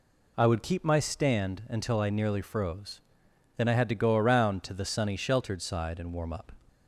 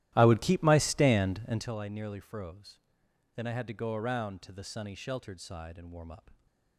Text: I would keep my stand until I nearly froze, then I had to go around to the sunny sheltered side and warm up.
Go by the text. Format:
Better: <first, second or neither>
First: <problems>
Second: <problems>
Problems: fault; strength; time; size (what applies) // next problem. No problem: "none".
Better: first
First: none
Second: starts louder than the rest; strong; until 1.7 s; 14 dB